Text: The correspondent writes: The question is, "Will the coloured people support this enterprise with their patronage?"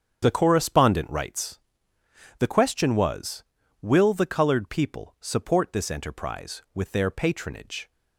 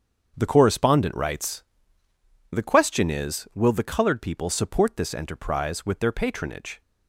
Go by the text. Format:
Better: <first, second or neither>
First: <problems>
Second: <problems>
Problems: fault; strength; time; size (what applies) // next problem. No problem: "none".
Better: second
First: starts louder than the rest; strong; until 1.2 s; 8.5 dB // says "was" for "is"; at 2.9 s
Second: starts louder than the rest; strong; until 1.3 s; 7 dB